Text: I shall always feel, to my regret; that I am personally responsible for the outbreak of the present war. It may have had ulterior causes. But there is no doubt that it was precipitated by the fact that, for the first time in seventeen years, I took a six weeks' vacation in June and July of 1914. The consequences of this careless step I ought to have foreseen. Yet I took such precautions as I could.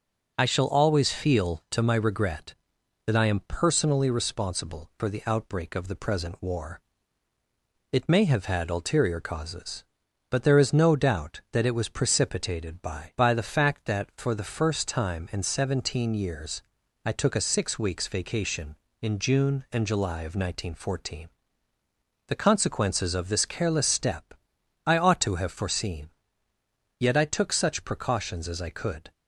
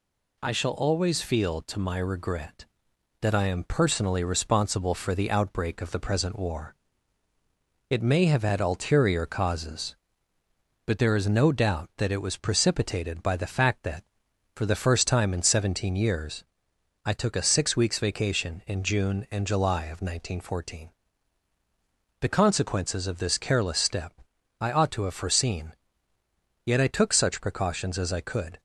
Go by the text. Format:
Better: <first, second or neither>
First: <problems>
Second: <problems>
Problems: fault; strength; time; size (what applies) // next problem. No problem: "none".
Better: second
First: says "by" twice; at 13.1 s // pauses between "step" and "I"; noticeable; at 24.3 s; 0.54 s long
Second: pauses between "step" and "I"; noticeable; at 24.1 s; 0.48 s long